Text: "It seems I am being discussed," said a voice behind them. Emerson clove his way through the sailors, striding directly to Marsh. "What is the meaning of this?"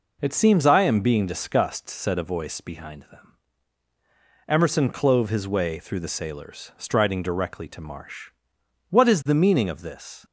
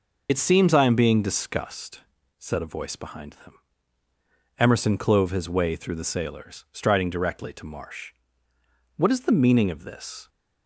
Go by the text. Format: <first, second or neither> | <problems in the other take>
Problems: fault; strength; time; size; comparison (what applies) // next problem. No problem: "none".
first | loses the start of "It"; at 0.2 s; 60 ms